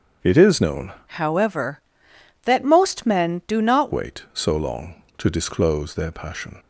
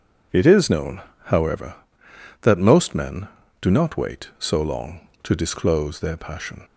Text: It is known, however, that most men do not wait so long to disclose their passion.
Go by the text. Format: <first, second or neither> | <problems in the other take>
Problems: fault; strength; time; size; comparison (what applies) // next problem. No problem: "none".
second | starts louder than the rest; until 1.3 s; 7 dB // changes voice from "however" to "not"; from 1.0 to 3.9 s; 2.9 s long